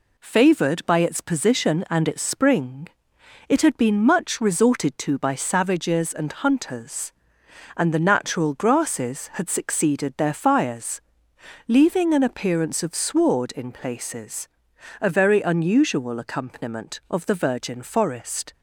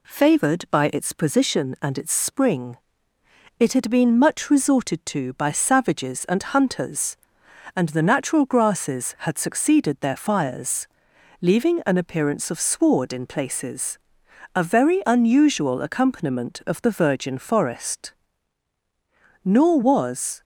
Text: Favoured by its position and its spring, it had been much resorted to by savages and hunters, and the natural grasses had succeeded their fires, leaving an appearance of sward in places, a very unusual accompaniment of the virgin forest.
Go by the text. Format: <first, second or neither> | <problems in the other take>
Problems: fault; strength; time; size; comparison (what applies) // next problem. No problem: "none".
first | goes on to say "Nor was"; noticeable; from 19.4 s on; 0.98 s long